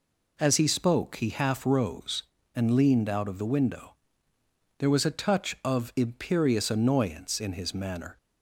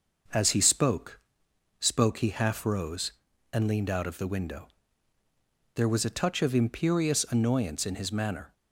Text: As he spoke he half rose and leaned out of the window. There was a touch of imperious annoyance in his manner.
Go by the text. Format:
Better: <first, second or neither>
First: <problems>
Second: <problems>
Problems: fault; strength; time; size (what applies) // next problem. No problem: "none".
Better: first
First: none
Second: says "spoke" twice; at 1.7 s